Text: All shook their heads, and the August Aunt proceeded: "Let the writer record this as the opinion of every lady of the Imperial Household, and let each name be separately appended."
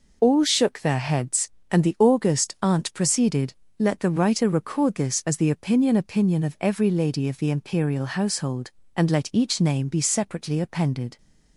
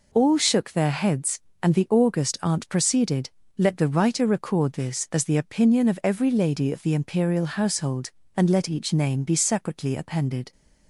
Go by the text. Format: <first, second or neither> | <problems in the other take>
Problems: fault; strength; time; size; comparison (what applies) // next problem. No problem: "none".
second | says "opinion" twice; at 5.9 s